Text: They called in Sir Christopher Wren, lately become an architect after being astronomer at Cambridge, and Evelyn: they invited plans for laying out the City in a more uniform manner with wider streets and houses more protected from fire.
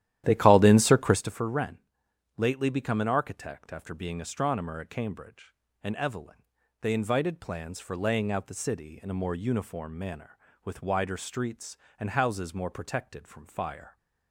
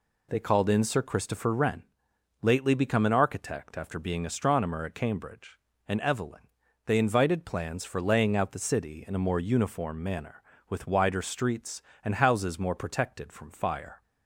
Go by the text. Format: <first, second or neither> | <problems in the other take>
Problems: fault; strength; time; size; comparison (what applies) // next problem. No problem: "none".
second | starts louder than the rest; strong; until 1.3 s; 12 dB